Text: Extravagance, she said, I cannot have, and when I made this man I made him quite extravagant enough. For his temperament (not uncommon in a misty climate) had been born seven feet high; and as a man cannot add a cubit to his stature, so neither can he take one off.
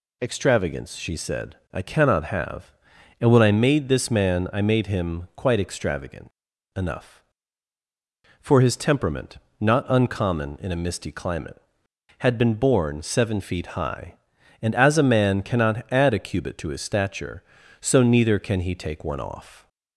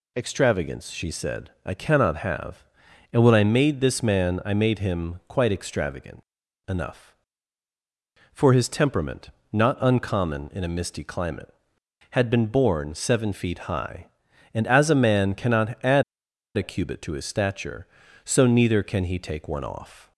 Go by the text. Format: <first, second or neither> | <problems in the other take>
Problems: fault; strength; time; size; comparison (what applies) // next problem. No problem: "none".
first | pauses between "extravagant" and "enough"; at 6.2 s; 0.44 s long; also in the first // pauses between "add" and "a"; noticeable; at 16.0 s; 0.54 s long